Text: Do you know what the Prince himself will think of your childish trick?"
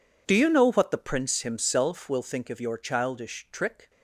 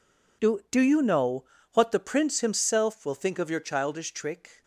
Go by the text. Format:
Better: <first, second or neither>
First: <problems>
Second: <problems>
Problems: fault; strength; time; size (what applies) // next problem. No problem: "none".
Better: first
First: none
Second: says "Do" twice; at 0.7 s // pauses between "know" and "what"; slight; at 1.4 s; 0.28 s long